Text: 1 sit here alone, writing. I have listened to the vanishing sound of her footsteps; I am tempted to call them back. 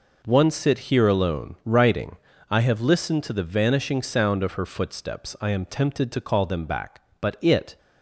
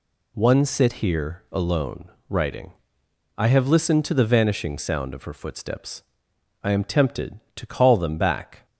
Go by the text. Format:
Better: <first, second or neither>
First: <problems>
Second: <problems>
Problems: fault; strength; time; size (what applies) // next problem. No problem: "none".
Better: second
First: goes on to say "But it"; from 7.2 s on; 0.56 s long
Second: none